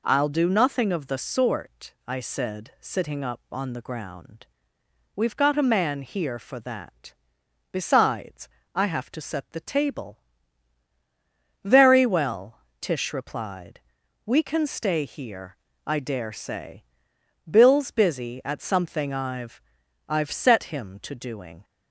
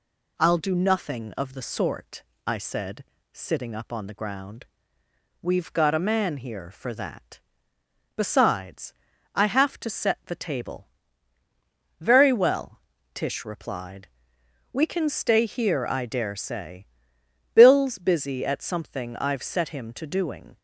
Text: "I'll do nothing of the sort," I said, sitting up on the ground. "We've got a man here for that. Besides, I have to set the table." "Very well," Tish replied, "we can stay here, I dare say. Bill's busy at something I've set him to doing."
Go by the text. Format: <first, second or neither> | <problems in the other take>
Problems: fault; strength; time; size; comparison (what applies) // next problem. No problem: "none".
second | says "I've" twice; at 20.0 s